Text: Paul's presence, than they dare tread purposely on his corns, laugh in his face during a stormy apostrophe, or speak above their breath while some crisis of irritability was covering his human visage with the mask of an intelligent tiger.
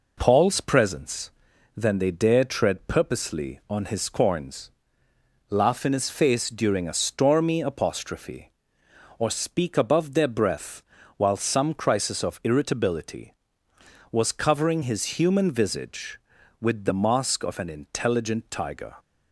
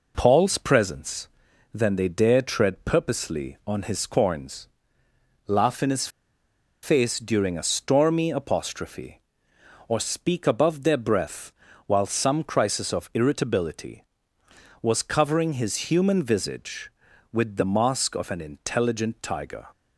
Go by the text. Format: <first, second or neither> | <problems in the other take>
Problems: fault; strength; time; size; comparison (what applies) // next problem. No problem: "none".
first | pauses between "his" and "face"; noticeable; at 6.0 s; 0.75 s long // pauses between "breath" and "while"; slight; at 11.5 s; 0.36 s long; slight in the first